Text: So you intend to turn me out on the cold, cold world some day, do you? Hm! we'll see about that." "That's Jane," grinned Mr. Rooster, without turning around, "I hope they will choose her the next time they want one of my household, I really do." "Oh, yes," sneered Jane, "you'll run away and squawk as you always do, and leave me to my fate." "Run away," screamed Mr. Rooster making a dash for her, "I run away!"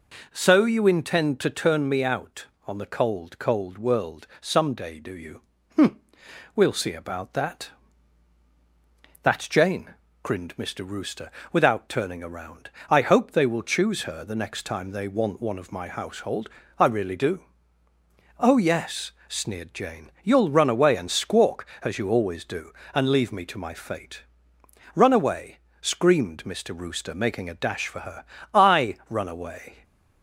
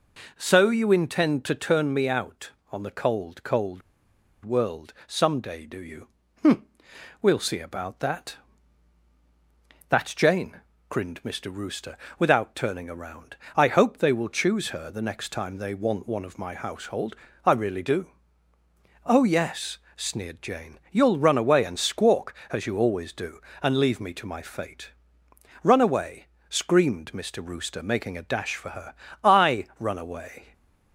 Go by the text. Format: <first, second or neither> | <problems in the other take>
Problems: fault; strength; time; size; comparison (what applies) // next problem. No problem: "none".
first | pauses between "cold" and "world"; noticeable; at 3.8 s; 0.63 s long